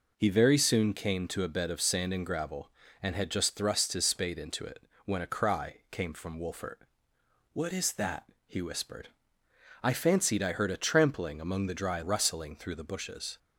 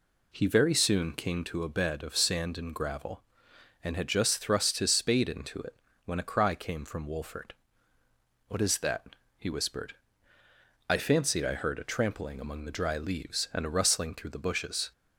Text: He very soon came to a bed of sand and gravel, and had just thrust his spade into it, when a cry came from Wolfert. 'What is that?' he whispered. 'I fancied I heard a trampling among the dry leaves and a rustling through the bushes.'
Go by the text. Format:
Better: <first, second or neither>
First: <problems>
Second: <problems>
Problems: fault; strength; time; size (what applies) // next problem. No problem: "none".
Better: second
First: skips "leaves and a"; at 12.0 s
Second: none